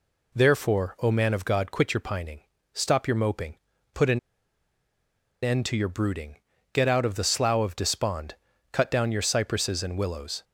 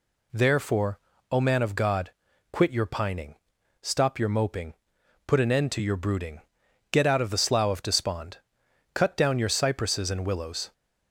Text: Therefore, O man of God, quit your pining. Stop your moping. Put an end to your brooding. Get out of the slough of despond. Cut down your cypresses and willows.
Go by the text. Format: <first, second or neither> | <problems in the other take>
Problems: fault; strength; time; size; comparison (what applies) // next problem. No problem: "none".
second | pauses between "an" and "end"; at 4.1 s; 1.2 s long